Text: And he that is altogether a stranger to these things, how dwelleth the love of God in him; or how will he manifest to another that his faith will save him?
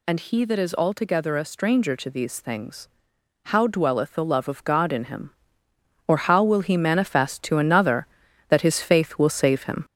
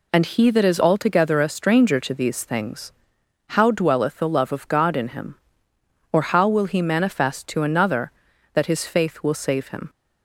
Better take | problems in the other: second | gets louder; noticeable; throughout; 4.5 dB

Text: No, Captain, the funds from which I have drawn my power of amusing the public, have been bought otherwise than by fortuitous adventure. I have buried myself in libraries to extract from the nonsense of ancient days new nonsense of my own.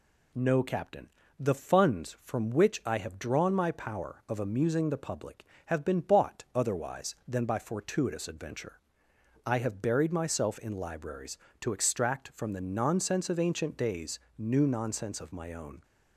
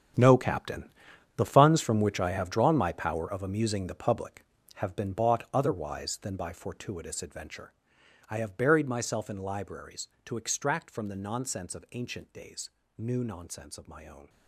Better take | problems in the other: first | gets quieter; strong; throughout; 13 dB // pauses between "days" and "new"; slight; at 12.6 s; 0.28 s long; slight in the first

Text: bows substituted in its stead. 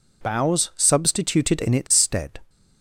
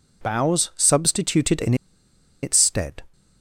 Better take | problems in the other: first | pauses between "in" and "its"; noticeable; at 1.7 s; 0.68 s long

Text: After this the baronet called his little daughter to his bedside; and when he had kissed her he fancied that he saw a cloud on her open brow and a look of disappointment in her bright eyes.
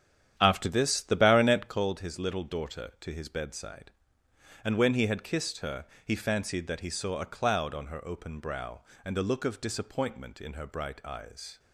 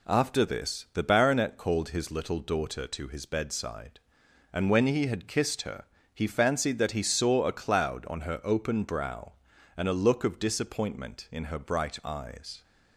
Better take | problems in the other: second | starts louder than the rest; strong; until 1.8 s; 9.5 dB // pauses between "her" and "he"; slight; at 5.8 s; 0.18 s long; slight in the second

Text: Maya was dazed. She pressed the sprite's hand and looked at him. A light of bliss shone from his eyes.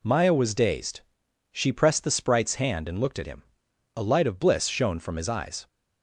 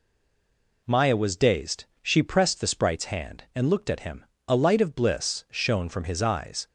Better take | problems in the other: first | stays silent before the first word; slight; until 0.8 s; 0.8 s long

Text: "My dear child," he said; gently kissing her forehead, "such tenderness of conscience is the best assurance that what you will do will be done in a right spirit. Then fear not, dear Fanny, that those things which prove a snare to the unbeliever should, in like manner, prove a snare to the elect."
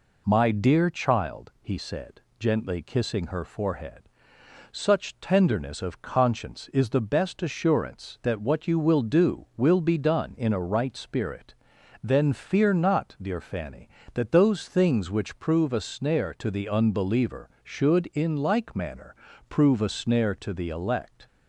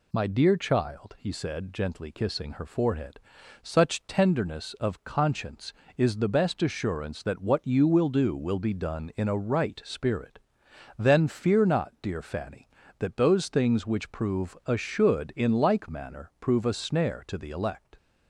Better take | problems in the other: first | skips "snare to the unbeliever"; at 14.7 s

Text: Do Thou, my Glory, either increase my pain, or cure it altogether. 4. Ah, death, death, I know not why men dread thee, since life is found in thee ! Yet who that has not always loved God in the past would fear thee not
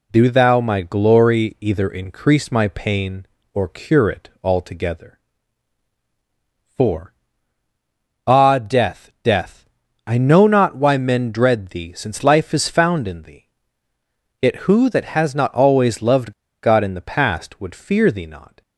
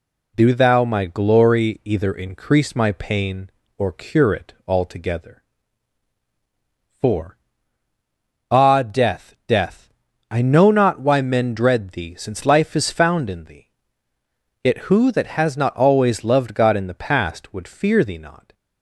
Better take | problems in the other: second | pauses between "loved" and "God"; slight; at 16.3 s; 0.30 s long

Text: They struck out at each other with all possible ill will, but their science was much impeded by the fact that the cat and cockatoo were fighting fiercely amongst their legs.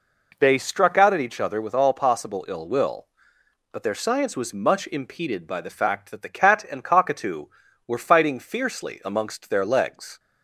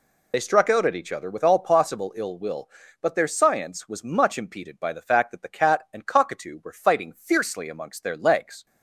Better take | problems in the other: first | loses the start of "They"; at 0.3 s; 45 ms

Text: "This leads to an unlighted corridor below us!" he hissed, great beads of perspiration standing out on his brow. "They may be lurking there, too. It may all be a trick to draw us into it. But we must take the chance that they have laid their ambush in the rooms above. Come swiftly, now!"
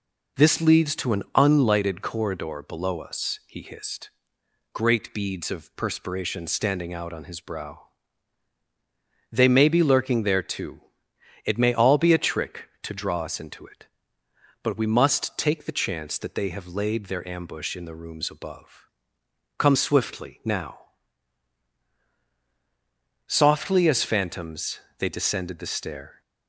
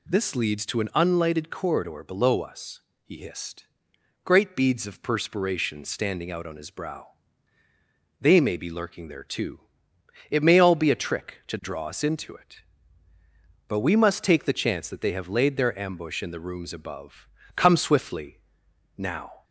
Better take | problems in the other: second | goes on to say "Softly as phantoms they descended the stair"; strong; from 23.2 s on; 2.9 s long

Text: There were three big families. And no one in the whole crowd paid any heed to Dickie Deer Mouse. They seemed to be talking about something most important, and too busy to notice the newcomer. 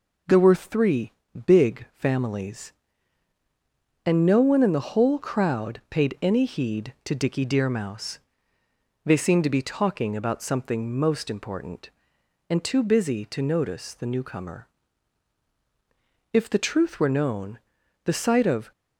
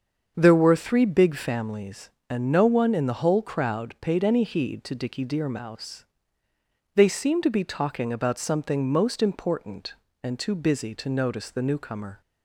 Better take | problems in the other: second | starts louder than the rest; until 1.6 s; 6.5 dB; also in the second // pauses between "three" and "big"; slight; at 1.1 s; 0.34 s long // goes on to say "If the truth were known the sight of"; strong; from 16.3 s on; 2.3 s long

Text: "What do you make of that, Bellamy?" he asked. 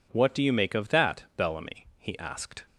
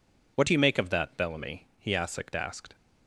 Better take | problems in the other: first | says "asked" twice; at 2.3 s

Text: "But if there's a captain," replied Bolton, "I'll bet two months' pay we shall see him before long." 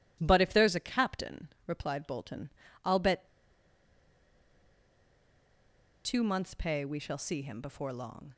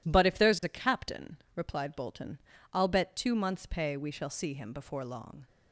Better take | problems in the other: second | pauses between "bet" and "two"; strong; at 3.2 s; 2.7 s long

